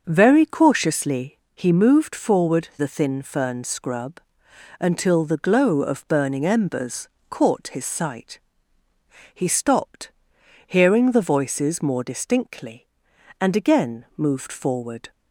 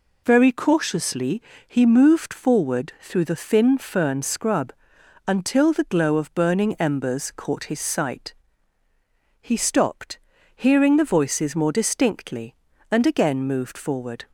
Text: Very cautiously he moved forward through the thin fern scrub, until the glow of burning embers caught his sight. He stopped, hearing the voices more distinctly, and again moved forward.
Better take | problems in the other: second | starts louder than the rest; until 1.0 s; 6.5 dB // pauses between "cautiously" and "he"; slight; at 1.3 s; 0.16 s long; slight in the second // skips "through"; at 2.7 s // pauses between "embers" and "caught"; slight; at 7.0 s; 0.22 s long

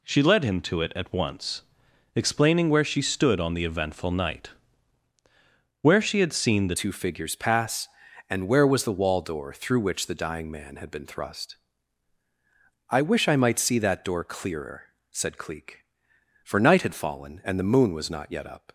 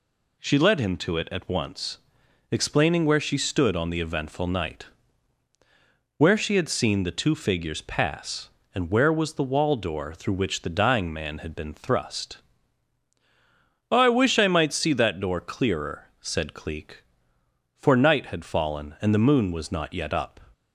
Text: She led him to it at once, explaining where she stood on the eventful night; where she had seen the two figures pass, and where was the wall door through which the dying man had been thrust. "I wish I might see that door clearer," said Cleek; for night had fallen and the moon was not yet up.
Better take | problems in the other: second | changes voice at "two"; from 6.7 s on; 12.0 s long

